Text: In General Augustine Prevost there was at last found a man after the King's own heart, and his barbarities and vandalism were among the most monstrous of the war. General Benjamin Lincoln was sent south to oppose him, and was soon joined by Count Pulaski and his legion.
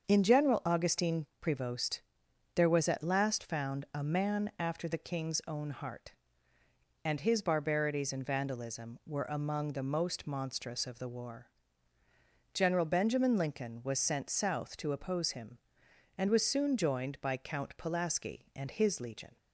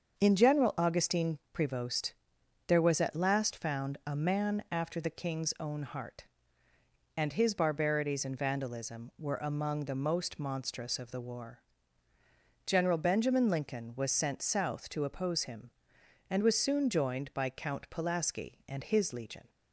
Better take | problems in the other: neither | starts louder than the rest; the same in both // pauses between "Augustine" and "Prevost"; slight; the same in both // pauses between "Prevost" and "there"; noticeable; the same in both

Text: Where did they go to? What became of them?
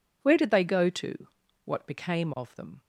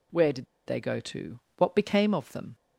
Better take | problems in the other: first | pauses between "did" and "they"; slight; at 0.4 s; 0.21 s long

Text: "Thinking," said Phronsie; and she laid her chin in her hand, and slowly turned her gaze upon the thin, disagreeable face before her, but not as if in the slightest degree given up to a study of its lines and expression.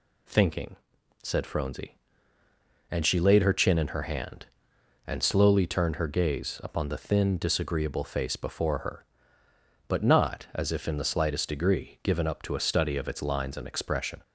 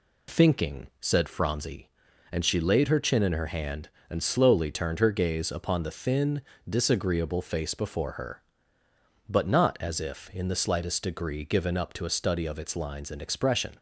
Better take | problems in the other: neither | none

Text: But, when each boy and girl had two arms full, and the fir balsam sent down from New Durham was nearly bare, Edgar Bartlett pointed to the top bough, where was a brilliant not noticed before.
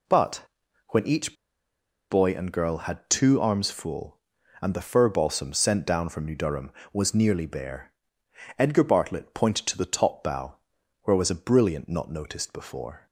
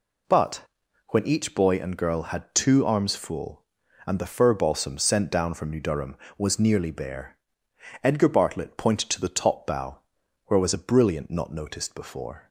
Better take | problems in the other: second | pauses between "each" and "boy"; noticeable; at 1.3 s; 0.77 s long

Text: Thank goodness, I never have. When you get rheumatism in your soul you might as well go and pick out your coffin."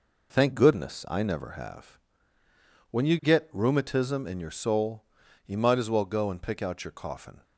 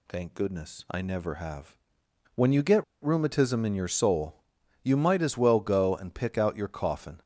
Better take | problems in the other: first | pauses between "get" and "rheumatism"; slight; at 2.8 s; 0.19 s long // pauses between "soul" and "you"; noticeable; at 4.3 s; 0.46 s long; also in the first

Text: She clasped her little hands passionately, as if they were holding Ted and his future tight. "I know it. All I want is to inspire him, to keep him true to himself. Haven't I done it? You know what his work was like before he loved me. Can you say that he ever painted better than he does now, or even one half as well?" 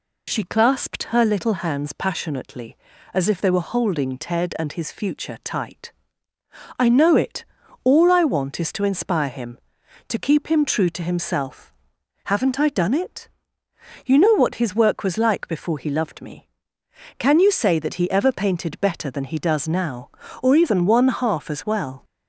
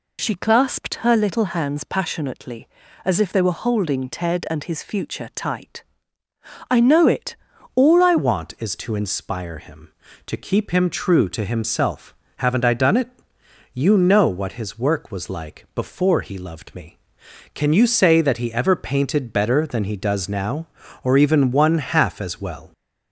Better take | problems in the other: first | changes voice at "want"; from 8.1 s on; 14.6 s long

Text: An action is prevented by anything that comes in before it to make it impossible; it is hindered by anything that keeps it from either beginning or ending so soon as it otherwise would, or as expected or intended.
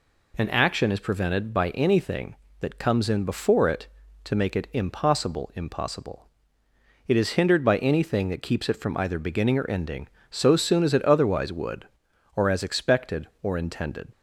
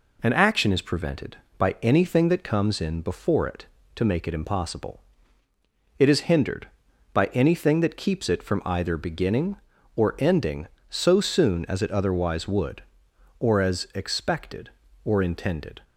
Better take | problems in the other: second | says "impossible" twice; at 5.5 s

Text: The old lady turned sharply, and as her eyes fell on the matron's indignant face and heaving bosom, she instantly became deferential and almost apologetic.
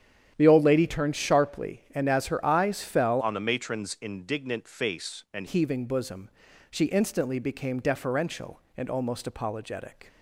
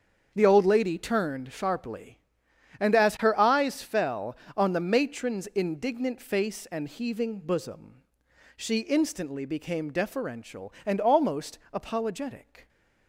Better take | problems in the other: second | starts louder than the rest; strong; until 1.3 s; 9 dB; also in the second // changes voice from "on" to "and"; from 3.2 to 5.4 s; 2.2 s long

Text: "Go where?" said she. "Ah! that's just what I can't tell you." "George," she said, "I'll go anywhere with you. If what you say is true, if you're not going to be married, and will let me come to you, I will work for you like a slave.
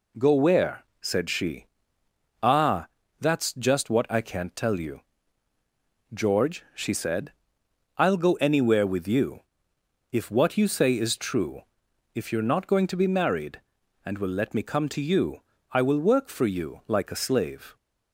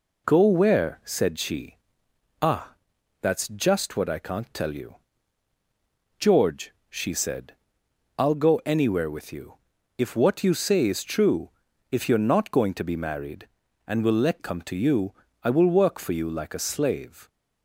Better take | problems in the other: first | skips "me"; at 14.3 s

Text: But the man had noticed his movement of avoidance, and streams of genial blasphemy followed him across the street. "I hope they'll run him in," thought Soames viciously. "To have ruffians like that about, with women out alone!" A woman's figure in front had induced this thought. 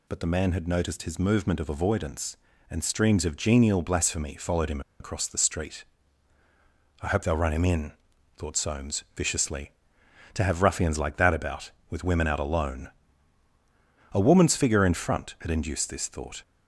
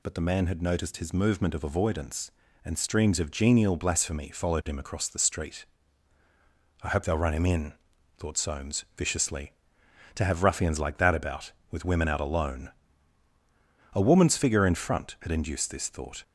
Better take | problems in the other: second | pauses between "him" and "across"; slight; at 4.8 s; 0.19 s long

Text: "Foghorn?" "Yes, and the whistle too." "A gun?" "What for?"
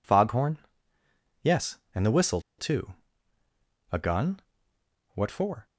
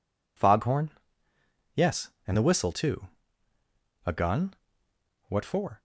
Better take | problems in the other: second | pauses between "whistle" and "too"; slight; at 2.3 s; 0.19 s long

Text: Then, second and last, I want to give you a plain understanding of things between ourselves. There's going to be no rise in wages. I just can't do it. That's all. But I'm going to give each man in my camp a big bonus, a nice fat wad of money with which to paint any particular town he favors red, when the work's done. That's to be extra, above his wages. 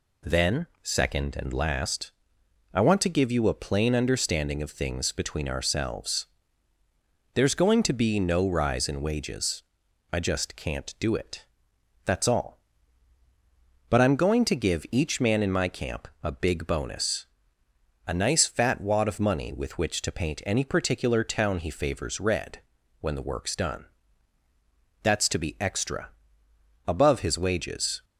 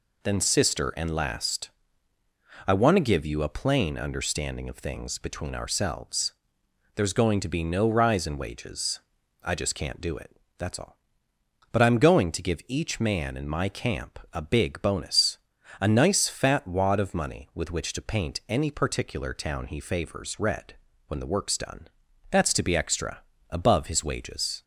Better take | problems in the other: first | says "sister" for "second"; at 0.4 s

